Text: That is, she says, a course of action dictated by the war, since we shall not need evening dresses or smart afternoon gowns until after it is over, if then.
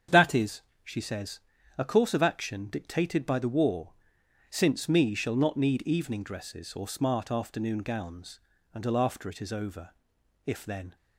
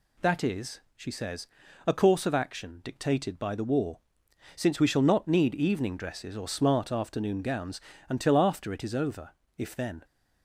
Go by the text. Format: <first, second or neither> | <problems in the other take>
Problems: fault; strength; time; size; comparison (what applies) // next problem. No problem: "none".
second | starts louder than the rest; strong; until 1.3 s; 8 dB // says "me" for "we"; at 4.8 s // pauses between "gowns" and "until"; slight; at 8.3 s; 0.34 s long; slight in the second